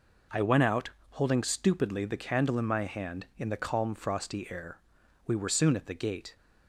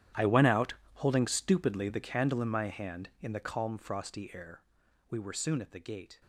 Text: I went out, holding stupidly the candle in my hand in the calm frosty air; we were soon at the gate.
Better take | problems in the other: first | gets quieter; strong; throughout; 18 dB

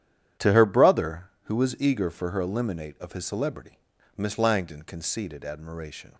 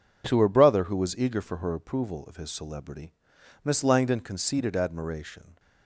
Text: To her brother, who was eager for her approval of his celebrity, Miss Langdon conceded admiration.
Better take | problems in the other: second | starts louder than the rest; strong; until 1.5 s; 10 dB // says "eliminate" for "approval"; at 2.4 s

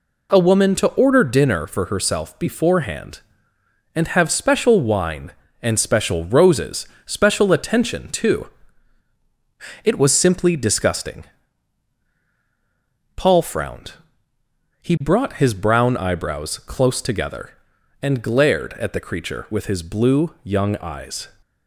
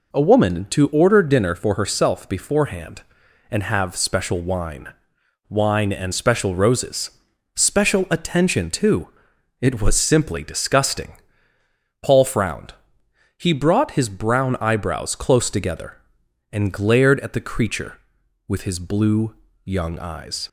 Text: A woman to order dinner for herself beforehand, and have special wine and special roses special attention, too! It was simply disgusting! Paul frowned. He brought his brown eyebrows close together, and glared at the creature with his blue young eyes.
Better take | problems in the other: first | says "wine" twice; at 5.4 s // pauses between "roses" and "special"; at 7.1 s; 0.44 s long; slight in the first // pauses between "blue" and "young"; slight; at 19.3 s; 0.30 s long

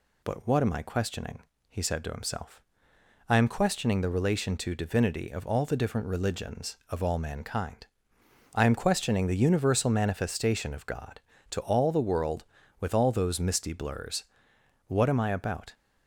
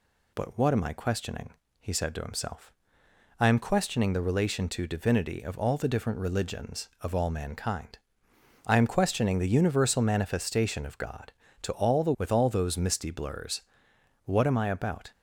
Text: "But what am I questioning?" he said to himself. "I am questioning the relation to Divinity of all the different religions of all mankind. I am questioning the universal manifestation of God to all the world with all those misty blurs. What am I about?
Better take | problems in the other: first | skips "world"; at 12.1 s

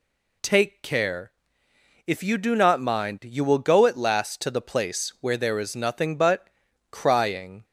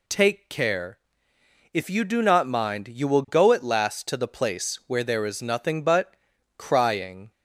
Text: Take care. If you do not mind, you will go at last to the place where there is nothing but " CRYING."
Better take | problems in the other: neither | none

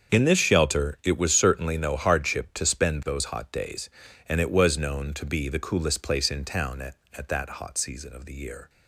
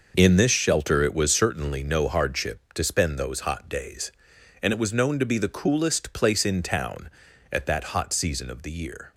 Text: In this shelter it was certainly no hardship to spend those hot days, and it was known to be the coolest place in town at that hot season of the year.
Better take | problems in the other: second | starts louder than the rest; strong; until 1.1 s; 7 dB // says "at" twice; at 7.1 s

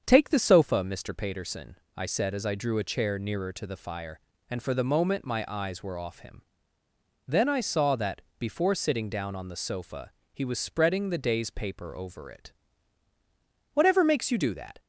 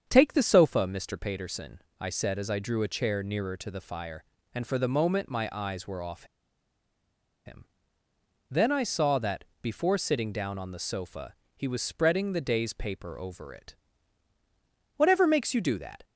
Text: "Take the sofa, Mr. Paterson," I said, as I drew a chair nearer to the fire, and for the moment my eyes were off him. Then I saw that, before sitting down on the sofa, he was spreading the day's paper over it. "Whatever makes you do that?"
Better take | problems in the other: first | starts louder than the rest; strong; until 1.0 s; 7.5 dB; strong in the first // pauses between "off" and "him"; at 6.2 s; 1.2 s long

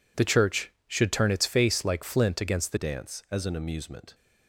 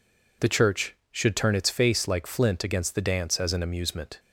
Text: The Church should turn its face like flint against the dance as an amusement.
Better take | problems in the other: second | changes voice at "dance"; from 2.7 s on; 1.4 s long

